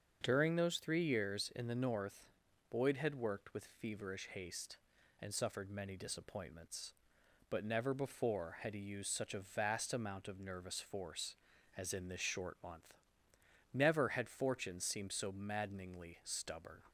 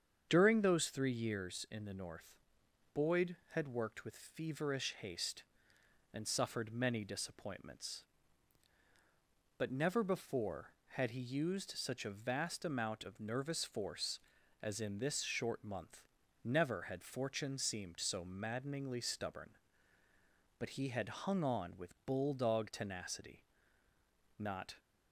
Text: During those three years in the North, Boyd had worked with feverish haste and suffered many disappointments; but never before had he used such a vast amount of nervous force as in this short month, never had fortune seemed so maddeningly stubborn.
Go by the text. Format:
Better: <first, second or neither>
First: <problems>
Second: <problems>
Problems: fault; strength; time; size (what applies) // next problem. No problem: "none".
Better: first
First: starts louder than the rest; until 1.2 s; 6.5 dB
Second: starts louder than the rest; strong; until 1.3 s; 7.5 dB // goes on to say "But he had hung on with bulldog tenacity not"; strong; from 20.5 s on; 4.1 s long